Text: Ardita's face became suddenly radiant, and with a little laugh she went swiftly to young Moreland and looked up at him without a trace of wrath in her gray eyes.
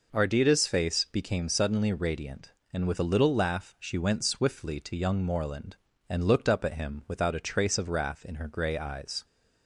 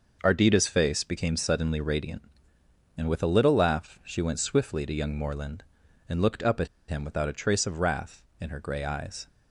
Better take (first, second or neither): first